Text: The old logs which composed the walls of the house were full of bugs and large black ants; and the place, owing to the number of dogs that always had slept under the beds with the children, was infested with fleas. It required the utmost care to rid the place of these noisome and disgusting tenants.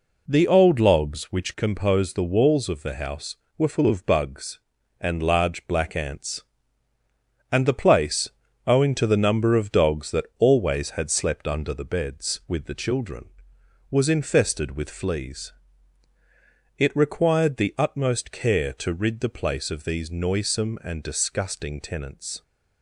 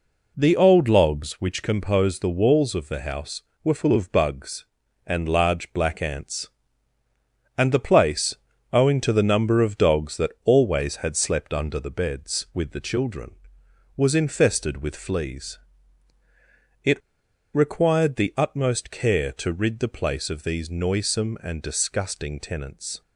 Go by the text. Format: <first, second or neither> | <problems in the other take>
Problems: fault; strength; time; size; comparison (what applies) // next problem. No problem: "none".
first | pauses between "It" and "required"; noticeable; at 17.0 s; 0.53 s long